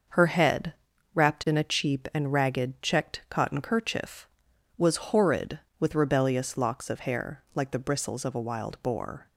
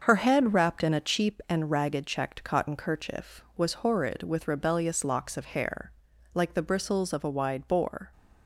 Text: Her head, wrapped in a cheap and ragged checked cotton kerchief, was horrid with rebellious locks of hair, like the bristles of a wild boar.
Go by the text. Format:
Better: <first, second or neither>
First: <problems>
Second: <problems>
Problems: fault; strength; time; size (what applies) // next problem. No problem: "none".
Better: first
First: starts louder than the rest; noticeable; until 1.5 s; 6 dB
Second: starts louder than the rest; until 1.0 s; 6.5 dB // says "wide" for "wild"; at 7.2 s